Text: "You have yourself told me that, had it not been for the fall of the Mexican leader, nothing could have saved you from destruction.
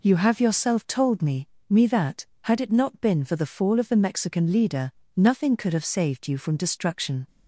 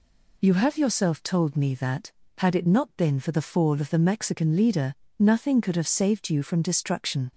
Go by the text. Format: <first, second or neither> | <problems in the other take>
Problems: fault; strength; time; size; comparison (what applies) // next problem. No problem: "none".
second | says "me" twice; at 1.6 s